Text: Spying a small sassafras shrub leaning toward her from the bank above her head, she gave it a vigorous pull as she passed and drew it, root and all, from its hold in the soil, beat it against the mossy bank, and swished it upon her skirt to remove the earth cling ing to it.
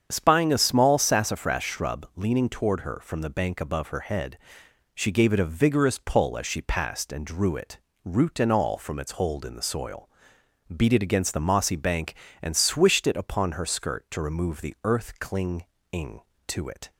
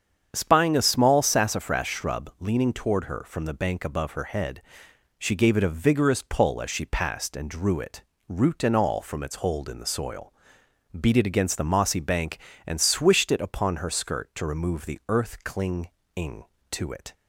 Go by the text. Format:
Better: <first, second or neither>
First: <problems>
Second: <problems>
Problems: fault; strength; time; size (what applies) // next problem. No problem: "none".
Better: neither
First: starts louder than the rest; strong; until 1.1 s; 8 dB // pauses between "cling" and "ing"; slight; at 15.6 s; 0.26 s long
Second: starts louder than the rest; strong; until 1.3 s; 8 dB // pauses between "cling" and "ing"; slight; at 15.8 s; 0.25 s long